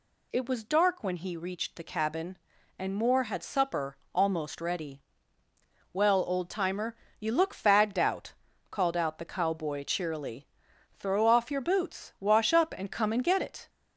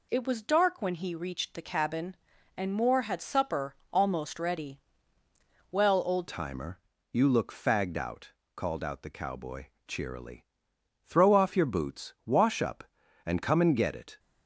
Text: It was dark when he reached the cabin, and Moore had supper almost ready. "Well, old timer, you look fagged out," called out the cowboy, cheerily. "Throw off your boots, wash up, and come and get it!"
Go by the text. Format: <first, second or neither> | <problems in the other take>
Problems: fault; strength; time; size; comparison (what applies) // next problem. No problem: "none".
first | pauses between "supper" and "almost"; slight; at 3.7 s; 0.18 s long; slight in the first // changes voice at "timer"; from 6.2 s on; 7.9 s long